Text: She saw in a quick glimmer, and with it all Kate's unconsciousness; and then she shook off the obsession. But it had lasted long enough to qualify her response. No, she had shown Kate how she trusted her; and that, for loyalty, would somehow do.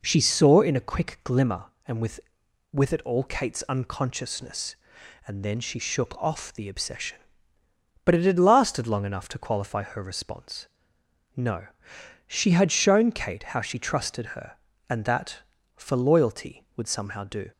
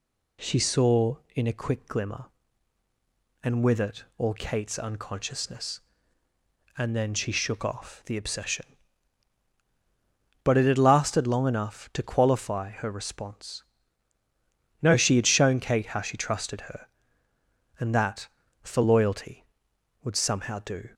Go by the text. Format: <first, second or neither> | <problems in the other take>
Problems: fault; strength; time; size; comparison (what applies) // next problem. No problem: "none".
second | says "with" twice; at 2.7 s